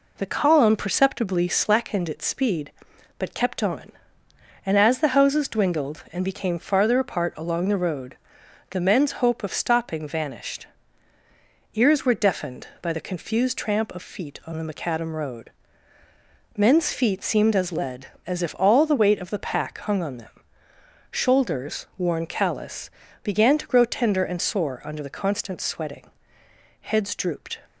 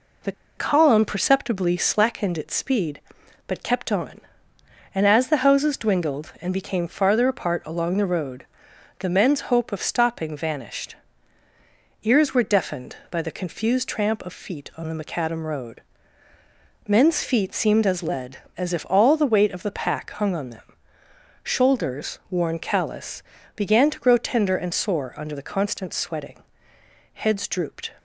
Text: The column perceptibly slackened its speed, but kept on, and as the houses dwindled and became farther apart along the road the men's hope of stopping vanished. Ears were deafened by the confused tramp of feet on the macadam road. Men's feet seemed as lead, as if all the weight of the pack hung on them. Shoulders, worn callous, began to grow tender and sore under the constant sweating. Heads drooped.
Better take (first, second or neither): first